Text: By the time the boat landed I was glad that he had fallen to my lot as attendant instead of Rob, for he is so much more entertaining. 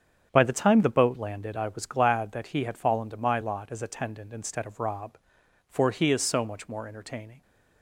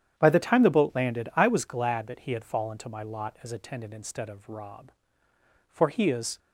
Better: first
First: starts louder than the rest; strong; until 1.3 s; 8 dB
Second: starts louder than the rest; strong; until 1.2 s; 9.5 dB // stops before "so much more entertaining"; at 6.3 s

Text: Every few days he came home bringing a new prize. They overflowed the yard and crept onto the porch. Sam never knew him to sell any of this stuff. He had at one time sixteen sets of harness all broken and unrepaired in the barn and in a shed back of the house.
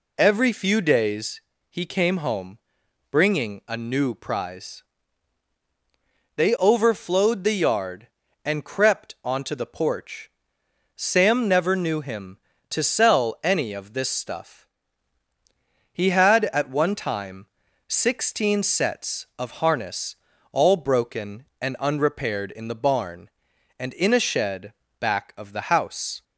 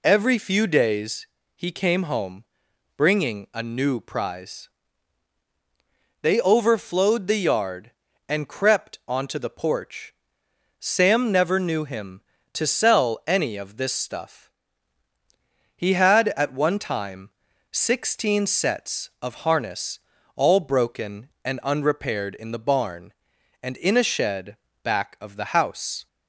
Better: neither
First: pauses between "days" and "he"; slight; at 1.4 s; 0.30 s long // pauses between "home" and "bringing"; noticeable; at 2.5 s; 0.52 s long // pauses between "time" and "sixteen"; at 17.4 s; 0.40 s long // pauses between "harness" and "all"; slight; at 20.1 s; 0.36 s long // pauses between "shed" and "back"; slight; at 24.7 s; 0.26 s long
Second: pauses between "days" and "he"; slight; at 1.2 s; 0.30 s long // pauses between "home" and "bringing"; noticeable; at 2.4 s; 0.52 s long // pauses between "time" and "sixteen"; at 17.3 s; 0.40 s long // pauses between "harness" and "all"; slight; at 19.9 s; 0.36 s long // pauses between "shed" and "back"; slight; at 24.5 s; 0.26 s long

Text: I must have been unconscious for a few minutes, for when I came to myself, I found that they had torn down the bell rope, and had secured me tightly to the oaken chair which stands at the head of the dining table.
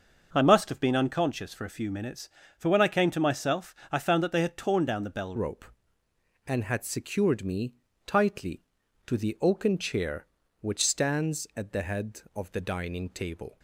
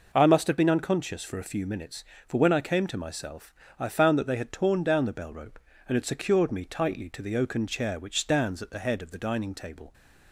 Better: second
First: starts louder than the rest; until 1.3 s; 6 dB // changes voice at "rope"; from 5.3 s on; 8.2 s long // pauses between "me" and "tightly"; slight; at 7.7 s; 0.32 s long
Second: none

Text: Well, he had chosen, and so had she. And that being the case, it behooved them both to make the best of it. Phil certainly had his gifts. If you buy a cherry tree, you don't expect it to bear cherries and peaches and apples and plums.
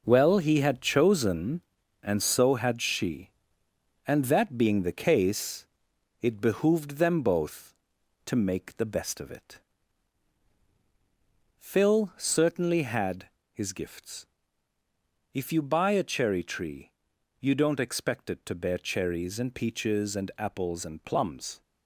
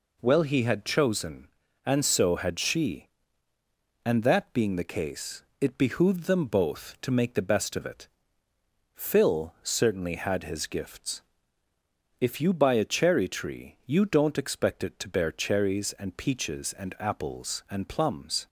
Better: second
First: gets quieter; strong; throughout; 8 dB // pauses between "had" and "his"; slight; at 13.2 s; 0.24 s long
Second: none

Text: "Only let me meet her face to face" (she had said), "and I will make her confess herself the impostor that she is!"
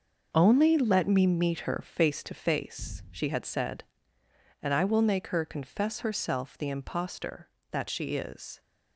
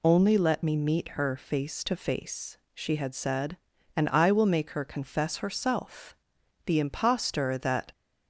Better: first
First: none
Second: pauses between "herself" and "the"; noticeable; at 6.1 s; 0.52 s long // stops before "she is"; at 7.9 s

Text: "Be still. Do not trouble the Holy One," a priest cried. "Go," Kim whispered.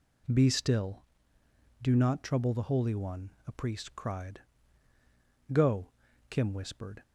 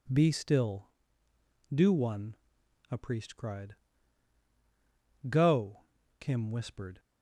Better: first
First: none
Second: skips "not trouble the Holy"; at 1.9 s

